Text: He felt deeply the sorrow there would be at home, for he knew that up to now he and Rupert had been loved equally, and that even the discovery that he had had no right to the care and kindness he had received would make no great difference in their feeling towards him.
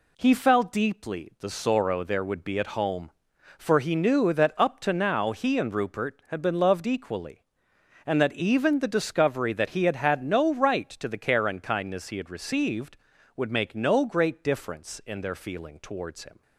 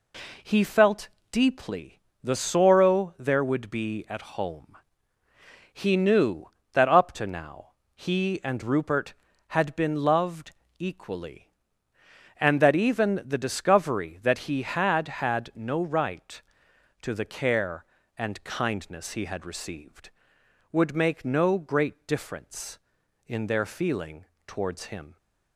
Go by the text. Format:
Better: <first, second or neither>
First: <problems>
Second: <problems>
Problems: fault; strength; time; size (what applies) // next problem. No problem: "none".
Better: first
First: none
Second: pauses between "felt" and "deeply"; slight; at 1.0 s; 0.24 s long // pauses between "deeply" and "the"; slight; at 1.9 s; 0.24 s long // skips "for"; at 5.2 s // pauses between "now" and "he"; slight; at 7.7 s; 0.22 s long // pauses between "loved" and "equally"; slight; at 10.5 s; 0.26 s long // pauses between "feeling" and "towards"; slight; at 24.2 s; 0.22 s long